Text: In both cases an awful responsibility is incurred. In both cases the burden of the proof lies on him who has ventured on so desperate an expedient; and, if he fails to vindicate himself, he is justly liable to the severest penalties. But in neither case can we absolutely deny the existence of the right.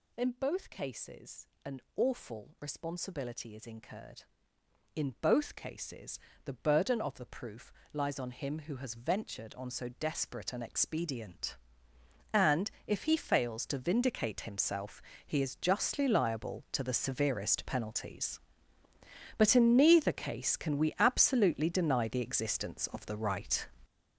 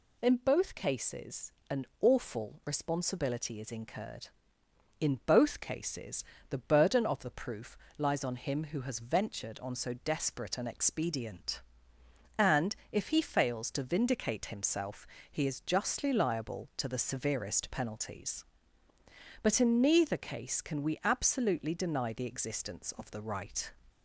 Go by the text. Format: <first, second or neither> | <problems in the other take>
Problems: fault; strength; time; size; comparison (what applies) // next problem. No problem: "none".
second | gets louder; strong; throughout; 10 dB // pauses between "cases" and "an"; slight; at 1.4 s; 0.18 s long; slight in the second // pauses between "an" and "awful"; slight; at 1.7 s; 0.16 s long; slight in the second // pauses between "cases" and "the"; slight; at 6.1 s; 0.26 s long; slight in the second // pauses between "proof" and "lies"; slight; at 7.7 s; 0.22 s long; slight in the second